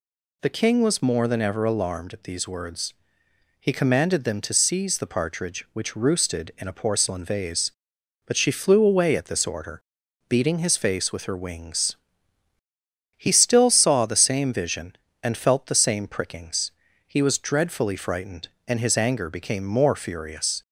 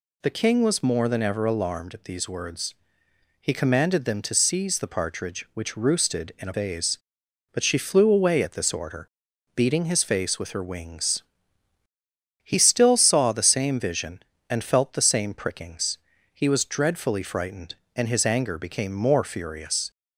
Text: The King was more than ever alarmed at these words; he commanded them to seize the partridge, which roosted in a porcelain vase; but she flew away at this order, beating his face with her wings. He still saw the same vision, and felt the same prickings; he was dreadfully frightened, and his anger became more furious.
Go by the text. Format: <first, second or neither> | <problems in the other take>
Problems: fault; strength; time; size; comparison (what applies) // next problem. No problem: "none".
first | skips "porcelain"; at 6.5 s